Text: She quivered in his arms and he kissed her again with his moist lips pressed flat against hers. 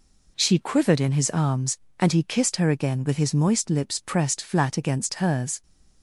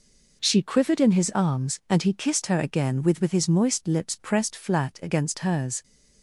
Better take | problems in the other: first | says "with" twice; at 3.2 s

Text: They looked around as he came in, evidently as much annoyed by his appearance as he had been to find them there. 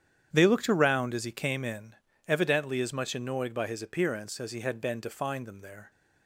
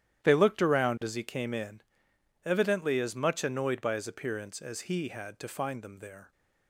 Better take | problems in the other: first | starts louder than the rest; strong; until 1.3 s; 12 dB; strong in the first // skips "been"; at 5.3 s

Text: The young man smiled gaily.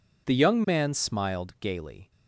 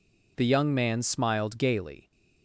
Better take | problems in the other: neither | none

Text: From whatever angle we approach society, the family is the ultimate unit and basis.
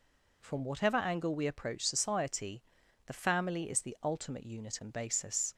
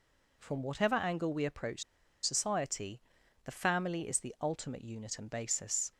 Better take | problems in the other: first | pauses between "approach" and "society"; at 1.8 s; 0.41 s long

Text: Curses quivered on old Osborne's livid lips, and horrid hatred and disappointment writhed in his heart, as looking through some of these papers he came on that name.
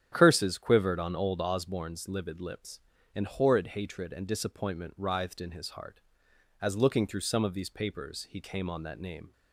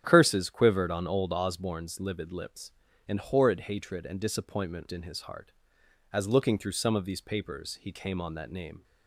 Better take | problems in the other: first | starts louder than the rest; strong; until 1.0 s; 9.5 dB; strong in the first // skips "writhed"; at 4.8 s

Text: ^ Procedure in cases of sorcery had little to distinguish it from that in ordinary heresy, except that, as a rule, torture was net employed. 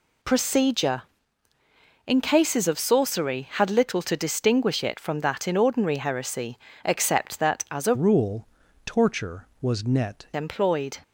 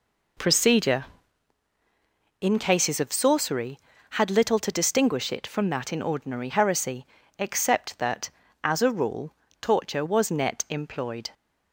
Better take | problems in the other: second | changes voice from "rule" to "net"; from 7.9 to 10.2 s; 2.3 s long

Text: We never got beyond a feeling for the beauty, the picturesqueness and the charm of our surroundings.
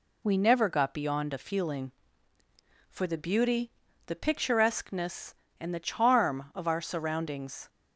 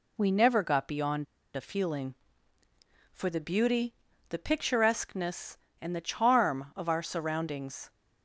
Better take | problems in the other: first | pauses between "beyond" and "a"; slight; at 1.2 s; 0.30 s long

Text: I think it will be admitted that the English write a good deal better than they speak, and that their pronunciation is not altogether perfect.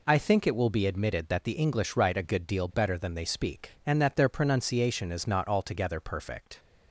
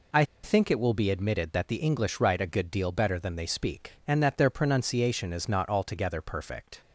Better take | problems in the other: first | pauses between "I" and "think"; slight; at 0.2 s; 0.20 s long

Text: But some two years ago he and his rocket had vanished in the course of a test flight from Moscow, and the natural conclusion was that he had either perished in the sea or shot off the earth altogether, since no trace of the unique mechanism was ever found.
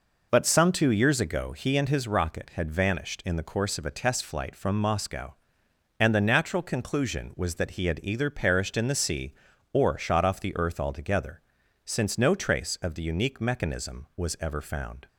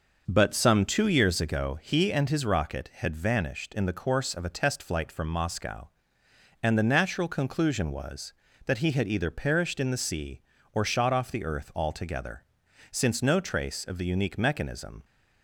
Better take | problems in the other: first | starts louder than the rest; until 1.2 s; 6 dB // stops before "was ever found"; at 15.0 s

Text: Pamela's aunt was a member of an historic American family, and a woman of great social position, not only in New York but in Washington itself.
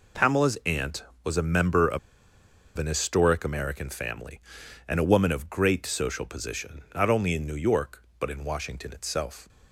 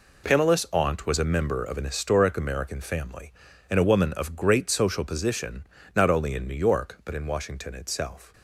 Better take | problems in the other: second | pauses between "of" and "an"; noticeable; at 1.9 s; 0.79 s long

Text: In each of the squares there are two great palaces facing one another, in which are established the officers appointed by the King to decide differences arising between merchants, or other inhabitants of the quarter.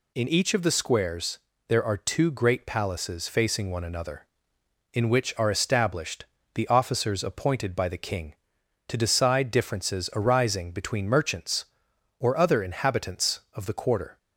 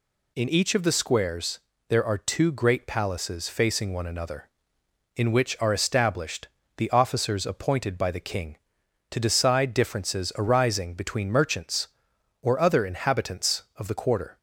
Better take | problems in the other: neither | pauses between "squares" and "there"; slight; the same in both // pauses between "established" and "the"; slight; the same in both

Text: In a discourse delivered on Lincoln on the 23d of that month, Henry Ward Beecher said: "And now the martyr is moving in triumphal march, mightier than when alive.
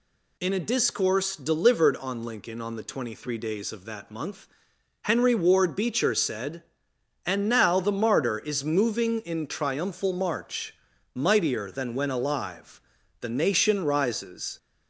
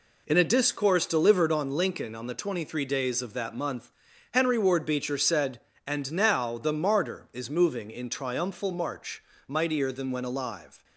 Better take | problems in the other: second | goes on to say "The nation rises"; from 13.1 s on; 1.3 s long

